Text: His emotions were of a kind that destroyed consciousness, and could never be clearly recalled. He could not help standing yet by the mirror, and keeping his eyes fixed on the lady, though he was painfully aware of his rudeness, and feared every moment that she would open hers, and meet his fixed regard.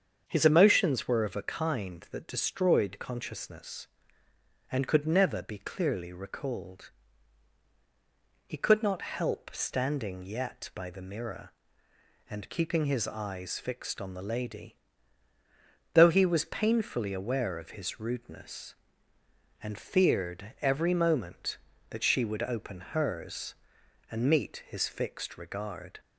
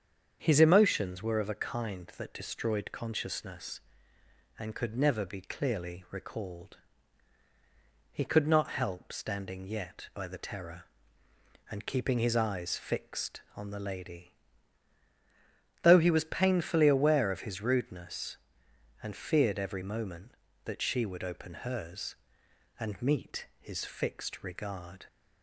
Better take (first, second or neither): first